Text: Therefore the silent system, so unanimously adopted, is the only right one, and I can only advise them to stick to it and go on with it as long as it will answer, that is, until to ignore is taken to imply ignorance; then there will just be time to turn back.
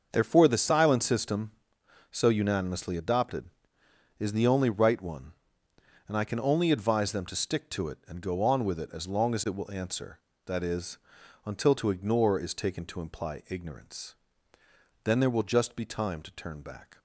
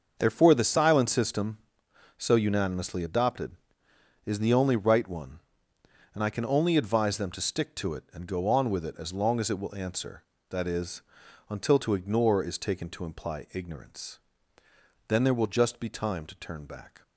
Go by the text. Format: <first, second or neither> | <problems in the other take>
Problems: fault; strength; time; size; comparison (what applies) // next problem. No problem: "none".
neither | starts louder than the rest; the same in both